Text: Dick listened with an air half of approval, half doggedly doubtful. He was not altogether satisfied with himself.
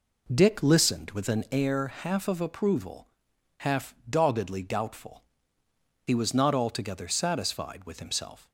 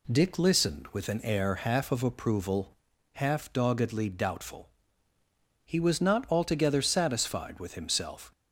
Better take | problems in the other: second | starts louder than the rest; noticeable; until 1.8 s; 4 dB

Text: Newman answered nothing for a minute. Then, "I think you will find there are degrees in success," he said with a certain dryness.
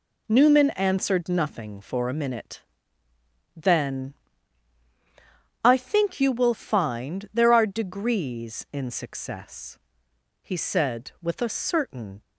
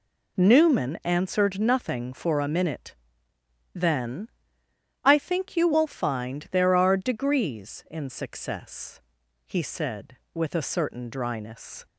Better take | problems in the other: second | stops before "dryness"; at 12.2 s

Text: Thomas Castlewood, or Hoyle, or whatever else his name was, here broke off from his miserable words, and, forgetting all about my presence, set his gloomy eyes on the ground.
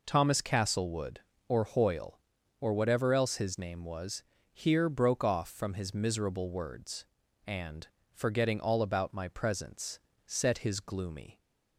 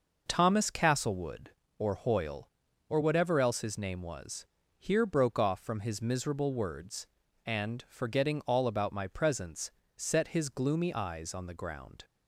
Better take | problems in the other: second | stops before "eyes on the ground"; at 11.3 s

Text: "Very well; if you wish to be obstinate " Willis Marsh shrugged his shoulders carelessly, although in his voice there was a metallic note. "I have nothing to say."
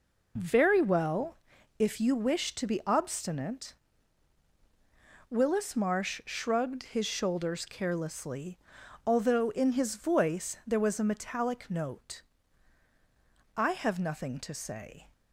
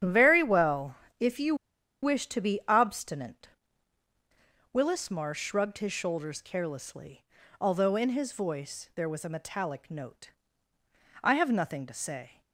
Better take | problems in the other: first | starts louder than the rest; strong; until 1.2 s; 10.5 dB // pauses between "you" and "wish"; noticeable; at 1.5 s; 0.47 s long

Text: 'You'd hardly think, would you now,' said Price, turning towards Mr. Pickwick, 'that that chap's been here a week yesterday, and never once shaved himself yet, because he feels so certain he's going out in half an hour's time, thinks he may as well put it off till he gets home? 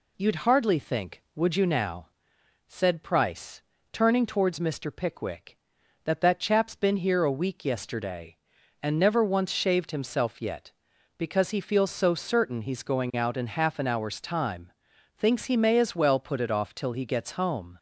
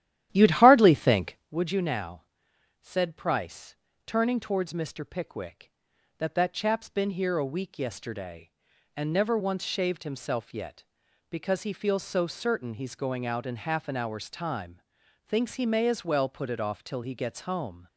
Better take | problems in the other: first | starts louder than the rest; strong; until 1.4 s; 12 dB

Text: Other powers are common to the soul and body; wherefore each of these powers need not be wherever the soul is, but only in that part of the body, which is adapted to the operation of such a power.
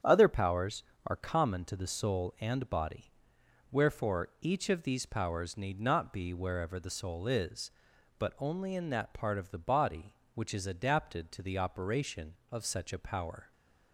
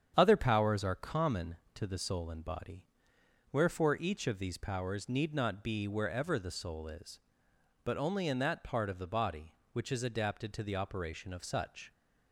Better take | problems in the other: first | starts louder than the rest; strong; until 1.1 s; 8.5 dB; strong in the first // stops before "a power"; at 11.9 s

